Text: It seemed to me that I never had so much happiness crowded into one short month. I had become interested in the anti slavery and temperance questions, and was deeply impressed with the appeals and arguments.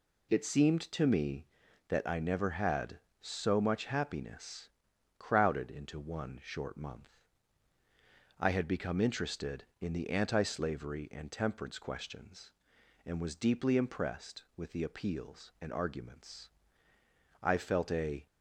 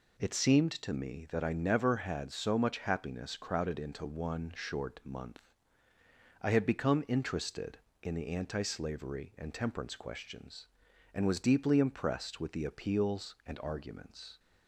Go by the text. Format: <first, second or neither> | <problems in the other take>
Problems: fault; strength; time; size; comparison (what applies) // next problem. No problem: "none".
second | pauses between "happiness" and "crowded"; noticeable; at 4.6 s; 0.48 s long // goes on to say "I felt a"; noticeable; from 17.4 s on; 0.84 s long